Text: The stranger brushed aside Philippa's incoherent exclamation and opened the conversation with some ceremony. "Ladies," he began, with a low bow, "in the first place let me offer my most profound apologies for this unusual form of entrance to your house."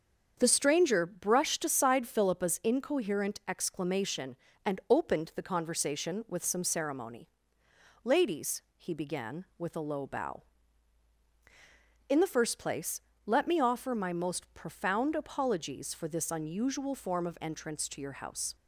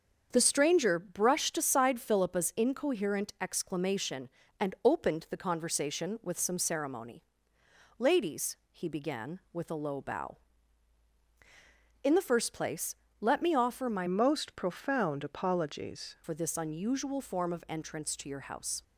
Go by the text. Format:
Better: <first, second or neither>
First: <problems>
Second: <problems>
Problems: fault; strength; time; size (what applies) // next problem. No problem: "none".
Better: first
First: starts louder than the rest; until 1.3 s; 7 dB // pauses between "place" and "let"; slight; at 13.0 s; 0.24 s long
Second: starts louder than the rest; until 1.3 s; 7 dB // pauses between "place" and "let"; slight; at 12.9 s; 0.24 s long // changes voice from "most" to "apologies"; from 14.0 to 16.1 s; 2.1 s long